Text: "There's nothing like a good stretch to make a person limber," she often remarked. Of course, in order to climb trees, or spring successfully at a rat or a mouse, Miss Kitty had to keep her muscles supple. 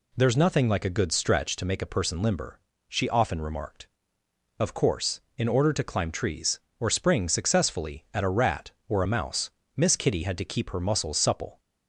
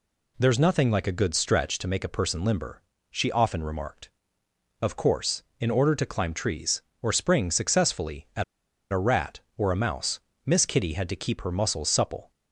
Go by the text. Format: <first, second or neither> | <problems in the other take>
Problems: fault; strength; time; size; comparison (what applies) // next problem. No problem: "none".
first | pauses between "at" and "a"; noticeable; at 8.4 s; 0.48 s long